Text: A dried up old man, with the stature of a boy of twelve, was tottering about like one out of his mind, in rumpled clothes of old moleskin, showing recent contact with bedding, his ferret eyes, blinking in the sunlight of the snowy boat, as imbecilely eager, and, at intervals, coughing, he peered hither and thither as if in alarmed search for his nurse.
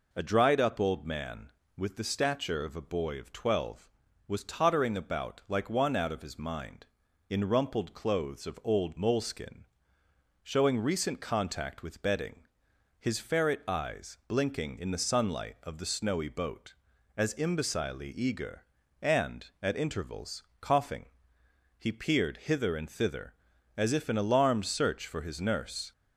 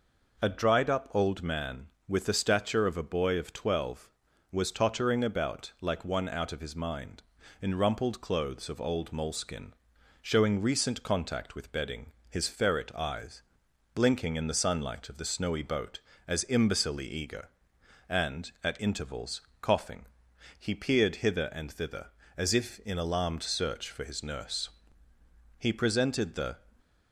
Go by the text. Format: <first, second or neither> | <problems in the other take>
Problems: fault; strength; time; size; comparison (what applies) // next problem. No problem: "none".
first | goes on to say "He presented the"; noticeable; from 25.5 s on; 1.0 s long